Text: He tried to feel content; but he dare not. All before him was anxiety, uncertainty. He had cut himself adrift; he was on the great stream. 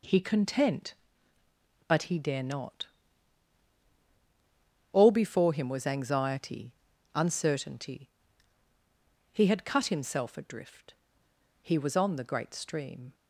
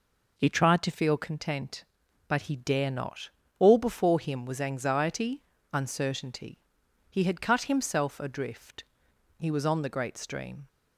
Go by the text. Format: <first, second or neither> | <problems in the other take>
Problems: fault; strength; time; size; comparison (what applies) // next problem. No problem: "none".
second | skips "tried to feel"; at 0.2 s